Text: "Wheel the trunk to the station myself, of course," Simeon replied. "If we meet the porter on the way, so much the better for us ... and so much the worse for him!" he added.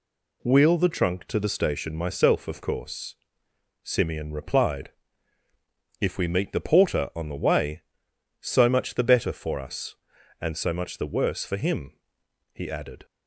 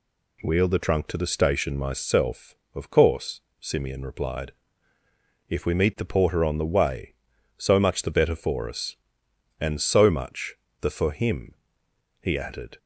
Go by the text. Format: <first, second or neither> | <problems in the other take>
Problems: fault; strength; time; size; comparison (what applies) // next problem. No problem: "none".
first | pauses between "much" and "the"; slight; at 10.5 s; 0.24 s long // skips "worse"; at 10.8 s